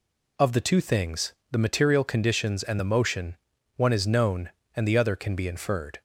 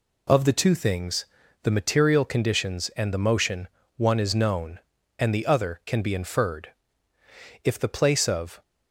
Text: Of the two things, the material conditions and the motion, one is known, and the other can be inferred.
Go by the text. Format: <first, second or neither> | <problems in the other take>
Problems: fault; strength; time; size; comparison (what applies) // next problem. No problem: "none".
first | goes on to say "If the place of"; noticeable; from 7.6 s on; 0.98 s long